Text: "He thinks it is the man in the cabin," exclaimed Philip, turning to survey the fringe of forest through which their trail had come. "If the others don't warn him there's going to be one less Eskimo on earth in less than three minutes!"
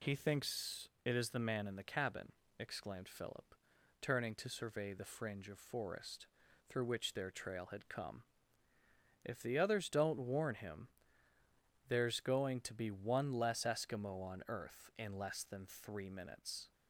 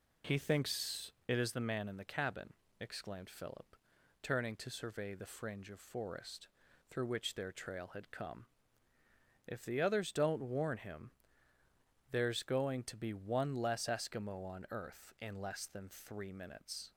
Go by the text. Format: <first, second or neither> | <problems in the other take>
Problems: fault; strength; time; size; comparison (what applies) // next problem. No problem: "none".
first | starts louder than the rest; slight; until 1.6 s; 3.5 dB // pauses between "thinks" and "it"; slight; at 1.1 s; 0.16 s long; slight in the first // pauses between "forest" and "through"; at 6.4 s; 0.42 s long; also in the first // pauses between "him" and "there's"; at 11.1 s; 1.0 s long; also in the first